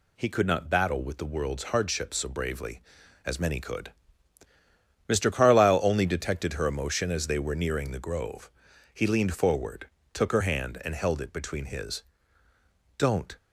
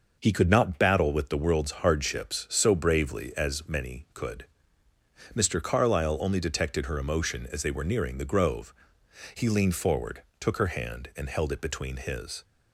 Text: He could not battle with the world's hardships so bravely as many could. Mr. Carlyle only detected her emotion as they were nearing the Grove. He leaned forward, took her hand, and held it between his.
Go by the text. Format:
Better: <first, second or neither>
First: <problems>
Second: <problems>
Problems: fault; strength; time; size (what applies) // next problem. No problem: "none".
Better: second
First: goes on to say "Don't"; slight; from 12.9 s on; 0.40 s long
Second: none